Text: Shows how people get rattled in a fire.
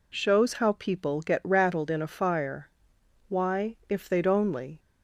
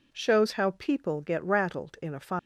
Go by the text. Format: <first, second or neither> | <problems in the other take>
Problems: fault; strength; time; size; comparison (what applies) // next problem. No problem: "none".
second | goes on to say "Why if they'd only"; from 3.2 s on; 1.5 s long